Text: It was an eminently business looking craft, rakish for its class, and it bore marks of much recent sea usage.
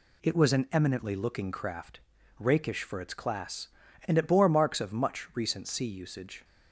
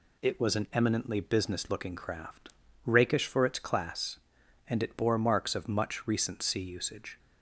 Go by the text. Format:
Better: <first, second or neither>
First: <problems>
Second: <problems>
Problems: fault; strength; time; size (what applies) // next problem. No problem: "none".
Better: second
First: skips "business"; at 1.1 s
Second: none